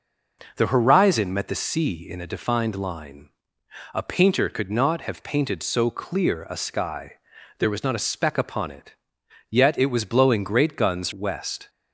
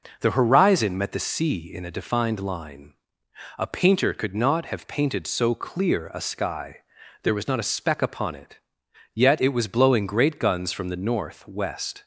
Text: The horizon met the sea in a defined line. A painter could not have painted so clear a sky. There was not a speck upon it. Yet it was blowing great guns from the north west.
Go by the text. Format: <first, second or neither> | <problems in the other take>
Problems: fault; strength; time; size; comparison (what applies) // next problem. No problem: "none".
second | skips "from the north"; at 11.1 s